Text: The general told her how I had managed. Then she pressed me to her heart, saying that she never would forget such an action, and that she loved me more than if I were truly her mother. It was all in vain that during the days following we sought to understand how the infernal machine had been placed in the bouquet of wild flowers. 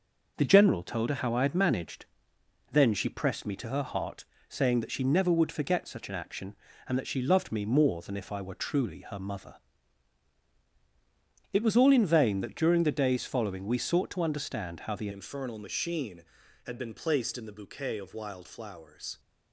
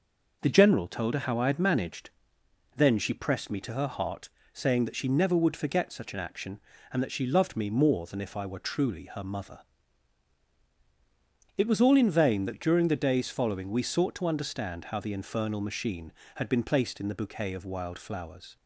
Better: second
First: changes voice at "infernal"; from 15.1 s on; 4.0 s long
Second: none

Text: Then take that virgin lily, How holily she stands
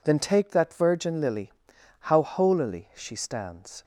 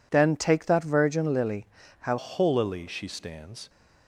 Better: first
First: none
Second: changes voice at "holily"; from 2.1 s on; 1.5 s long

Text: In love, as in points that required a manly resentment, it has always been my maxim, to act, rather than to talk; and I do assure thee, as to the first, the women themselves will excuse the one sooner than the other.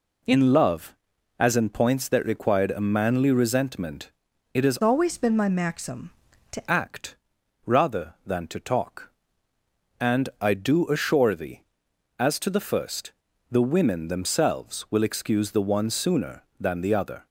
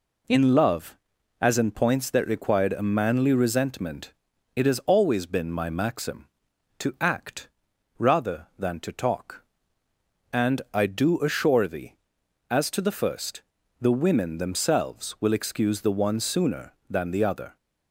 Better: second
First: changes voice from "always" to "to"; from 4.8 to 6.6 s; 1.8 s long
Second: none

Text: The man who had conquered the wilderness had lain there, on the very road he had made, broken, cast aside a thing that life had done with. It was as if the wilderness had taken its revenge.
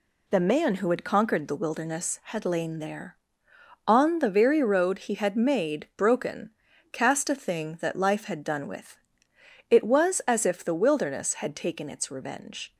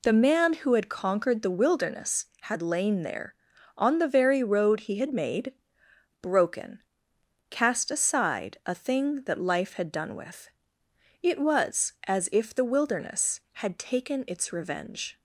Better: second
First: skips "aside"; at 7.2 s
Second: none

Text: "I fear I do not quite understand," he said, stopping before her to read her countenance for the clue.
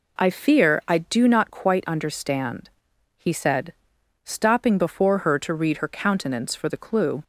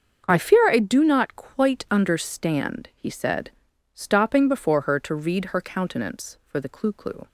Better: first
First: none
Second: starts louder than the rest; until 1.2 s; 7 dB // says "clue" twice; at 6.9 s

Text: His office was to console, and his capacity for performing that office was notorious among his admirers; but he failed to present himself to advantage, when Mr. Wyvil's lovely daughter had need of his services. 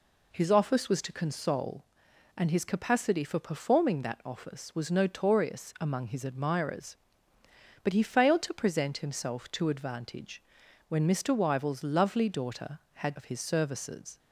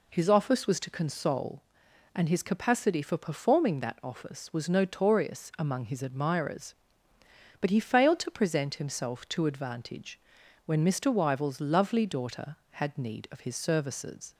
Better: second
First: skips "need"; at 13.1 s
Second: none

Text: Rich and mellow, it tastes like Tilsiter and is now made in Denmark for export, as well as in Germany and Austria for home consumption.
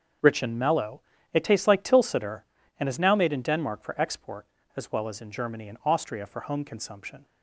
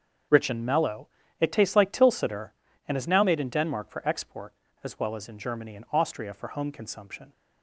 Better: neither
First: starts louder than the rest; strong; until 1.5 s; 7 dB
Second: starts louder than the rest; strong; until 1.6 s; 7 dB

